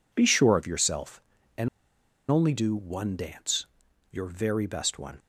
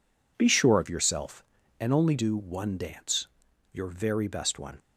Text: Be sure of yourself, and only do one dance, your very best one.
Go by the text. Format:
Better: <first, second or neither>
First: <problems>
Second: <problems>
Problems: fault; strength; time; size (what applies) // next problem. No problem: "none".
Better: second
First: pauses between "and" and "only"; noticeable; at 1.6 s; 0.61 s long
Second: none